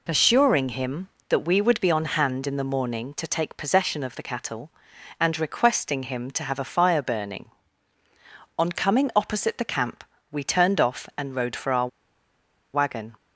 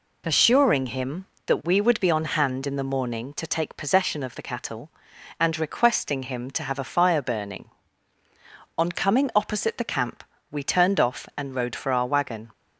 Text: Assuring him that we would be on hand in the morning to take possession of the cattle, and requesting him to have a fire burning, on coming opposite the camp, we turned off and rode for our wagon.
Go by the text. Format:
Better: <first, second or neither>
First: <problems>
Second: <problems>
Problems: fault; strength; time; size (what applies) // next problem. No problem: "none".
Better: second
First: pauses between "our" and "wagon"; noticeable; at 11.8 s; 0.86 s long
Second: none